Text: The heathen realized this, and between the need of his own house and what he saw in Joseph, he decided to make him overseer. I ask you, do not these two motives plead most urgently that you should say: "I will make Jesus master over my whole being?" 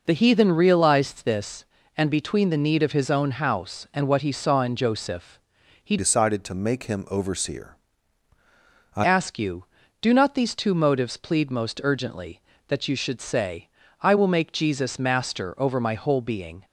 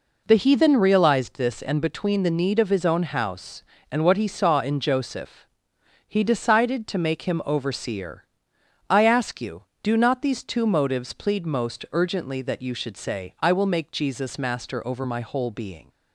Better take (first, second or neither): second